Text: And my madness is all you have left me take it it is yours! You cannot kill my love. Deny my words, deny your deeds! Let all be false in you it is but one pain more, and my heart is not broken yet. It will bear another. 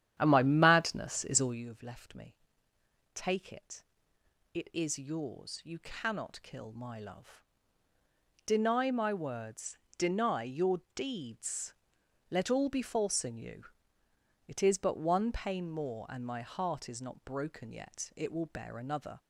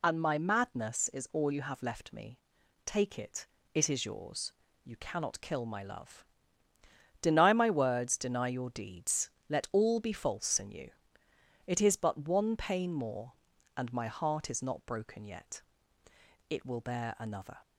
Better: second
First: starts louder than the rest; strong; until 1.7 s; 10 dB // pauses between "me" and "take"; noticeable; at 2.3 s; 0.78 s long // pauses between "it" and "it"; noticeable; at 3.8 s; 0.70 s long // pauses between "you" and "it"; noticeable; at 13.6 s; 0.82 s long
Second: pauses between "me" and "take"; noticeable; at 2.3 s; 0.48 s long // pauses between "it" and "it"; slight; at 3.4 s; 0.26 s long // pauses between "you" and "it"; noticeable; at 10.8 s; 0.76 s long

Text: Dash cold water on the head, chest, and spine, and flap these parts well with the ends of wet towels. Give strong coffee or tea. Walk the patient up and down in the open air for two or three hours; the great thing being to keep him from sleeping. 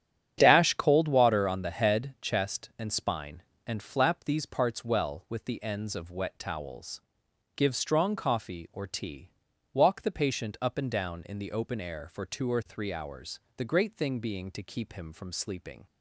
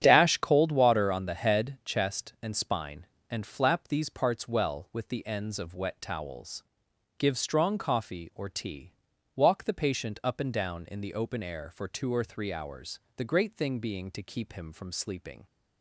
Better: neither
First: starts louder than the rest; strong; until 1.3 s; 10 dB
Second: starts louder than the rest; strong; until 1.0 s; 9.5 dB

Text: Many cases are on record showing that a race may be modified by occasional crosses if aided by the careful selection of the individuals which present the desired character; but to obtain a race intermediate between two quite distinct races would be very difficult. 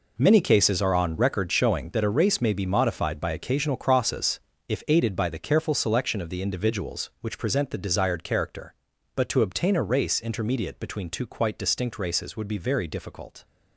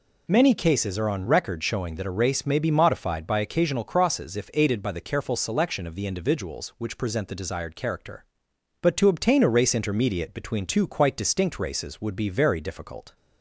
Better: second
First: gets quieter; strong; throughout; 11.5 dB // pauses between "crosses" and "if"; slight; at 4.3 s; 0.30 s long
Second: none

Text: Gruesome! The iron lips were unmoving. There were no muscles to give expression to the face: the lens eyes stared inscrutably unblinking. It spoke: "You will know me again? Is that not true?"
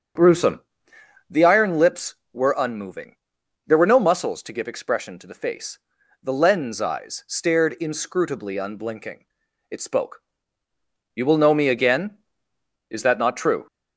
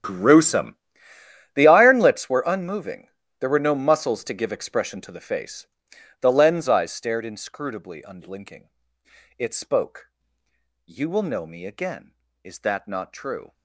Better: first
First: starts louder than the rest; strong; until 1.8 s; 7 dB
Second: gets quieter; strong; throughout; 18 dB // starts louder than the rest; strong; until 1.8 s; 10 dB

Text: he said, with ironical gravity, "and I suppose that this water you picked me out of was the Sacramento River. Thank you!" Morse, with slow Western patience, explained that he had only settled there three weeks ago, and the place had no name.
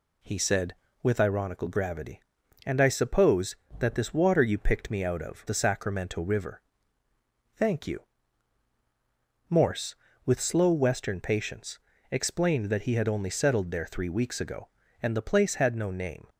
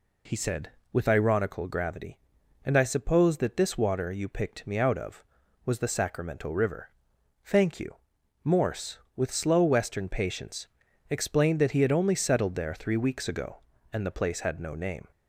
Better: second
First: skips "was"; at 5.4 s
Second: none

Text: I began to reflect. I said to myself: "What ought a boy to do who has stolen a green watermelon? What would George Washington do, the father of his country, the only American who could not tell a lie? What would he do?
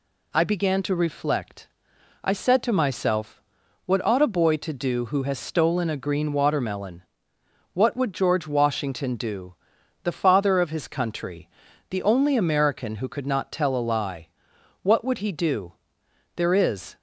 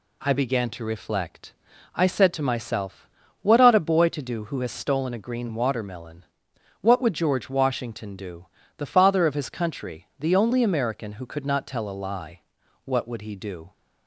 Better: second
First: goes on to say "There is"; from 16.3 s on; 0.60 s long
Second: none

